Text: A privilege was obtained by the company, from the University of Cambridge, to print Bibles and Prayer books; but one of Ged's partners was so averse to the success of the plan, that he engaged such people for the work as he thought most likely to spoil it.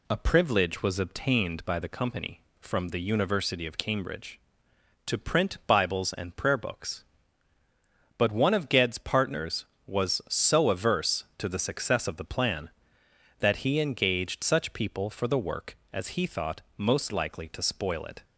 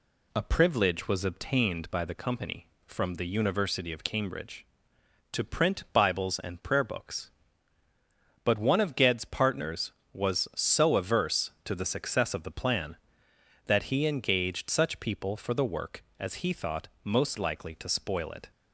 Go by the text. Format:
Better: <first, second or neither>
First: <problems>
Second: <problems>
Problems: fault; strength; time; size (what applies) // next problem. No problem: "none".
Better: neither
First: pauses between "thought" and "most"; slight; at 16.6 s; 0.16 s long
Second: pauses between "thought" and "most"; slight; at 16.8 s; 0.16 s long